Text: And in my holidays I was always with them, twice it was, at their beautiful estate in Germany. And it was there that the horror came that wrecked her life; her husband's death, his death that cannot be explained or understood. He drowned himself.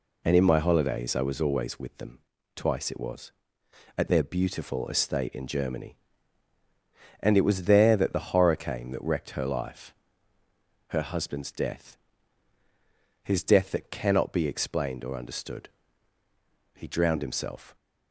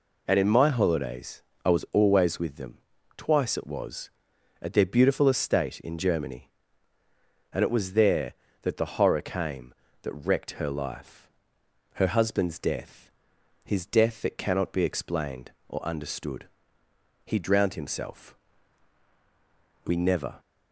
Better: first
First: none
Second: pauses between "holidays" and "I"; slight; at 1.4 s; 0.22 s long // goes on to say "We never"; from 19.8 s on; 0.54 s long

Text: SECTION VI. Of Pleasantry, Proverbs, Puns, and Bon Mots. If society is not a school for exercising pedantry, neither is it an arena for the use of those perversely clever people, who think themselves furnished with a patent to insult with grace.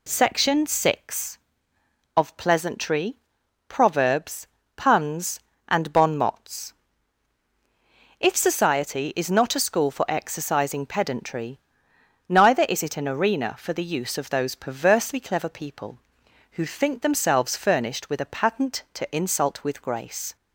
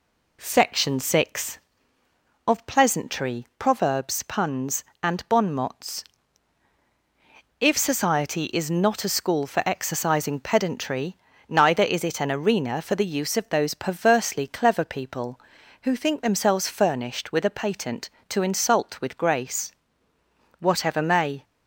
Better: first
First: none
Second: goes on to say "Whatever may"; noticeable; from 20.5 s on; 0.86 s long

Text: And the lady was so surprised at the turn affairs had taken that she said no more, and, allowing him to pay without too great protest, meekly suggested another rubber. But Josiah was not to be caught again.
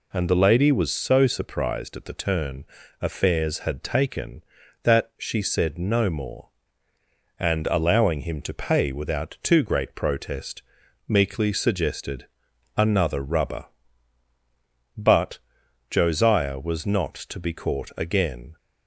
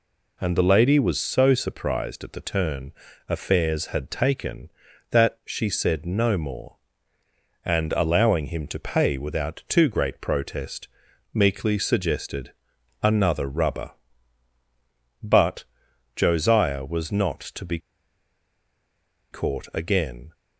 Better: first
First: pauses between "turn" and "affairs"; slight; at 2.6 s; 0.36 s long // pauses between "suggested" and "another"; noticeable; at 12.2 s; 0.50 s long // pauses between "But" and "Josiah"; noticeable; at 15.3 s; 0.52 s long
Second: pauses between "turn" and "affairs"; slight; at 2.9 s; 0.36 s long // pauses between "suggested" and "another"; noticeable; at 12.5 s; 0.50 s long // pauses between "But" and "Josiah"; noticeable; at 15.6 s; 0.52 s long // pauses between "be" and "caught"; strong; at 17.7 s; 1.5 s long

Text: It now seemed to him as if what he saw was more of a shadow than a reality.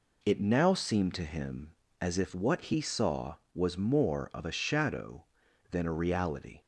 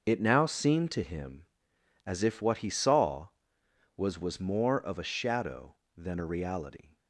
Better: first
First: none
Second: starts louder than the rest; noticeable; until 1.0 s; 6 dB // says "was" twice; at 4.1 s

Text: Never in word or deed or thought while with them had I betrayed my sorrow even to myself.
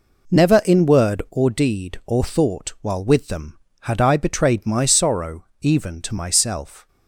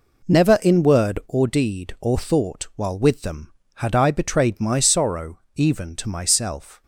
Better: neither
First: pauses between "sorrow" and "even"; slight; at 5.4 s; 0.16 s long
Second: pauses between "sorrow" and "even"; slight; at 5.3 s; 0.16 s long

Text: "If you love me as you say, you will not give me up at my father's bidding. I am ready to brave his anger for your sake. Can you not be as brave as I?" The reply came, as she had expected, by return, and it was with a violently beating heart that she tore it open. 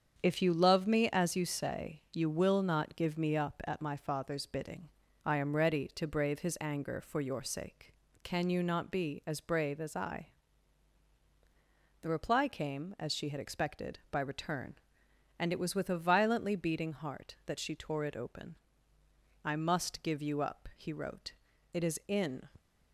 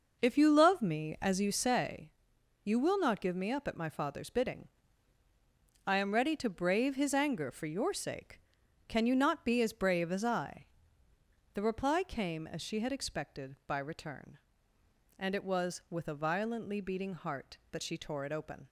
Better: second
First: starts louder than the rest; strong; until 1.2 s; 7.5 dB // goes on to say "I must give you up he wrote It is in"; strong; from 19.4 s on; 3.0 s long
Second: none

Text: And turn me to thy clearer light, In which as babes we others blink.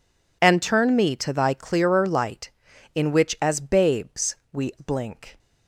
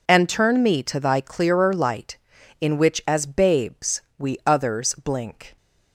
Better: second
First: pauses between "babes" and "we"; slight; at 4.3 s; 0.16 s long // skips "others"; at 4.7 s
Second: pauses between "babes" and "we"; slight; at 4.0 s; 0.16 s long

